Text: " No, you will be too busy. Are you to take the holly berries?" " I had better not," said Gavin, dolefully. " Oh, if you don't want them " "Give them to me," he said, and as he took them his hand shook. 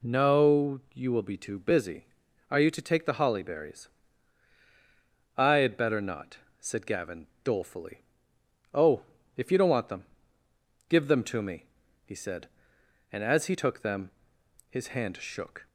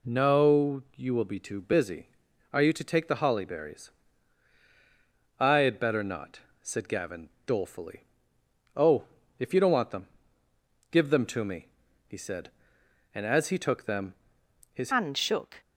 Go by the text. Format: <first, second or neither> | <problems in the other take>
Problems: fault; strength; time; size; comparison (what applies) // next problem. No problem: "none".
first | pauses between "them" and "his"; noticeable; at 14.1 s; 0.62 s long; noticeable in the first // changes voice at "hand"; from 14.9 s on; 0.7 s long